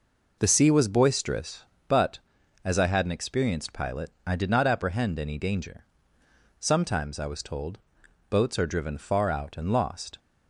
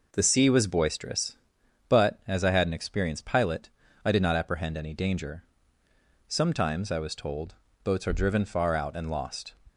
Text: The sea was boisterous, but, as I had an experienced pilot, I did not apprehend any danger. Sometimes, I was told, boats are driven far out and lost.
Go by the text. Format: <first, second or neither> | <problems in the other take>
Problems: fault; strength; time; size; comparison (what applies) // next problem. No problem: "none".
neither | none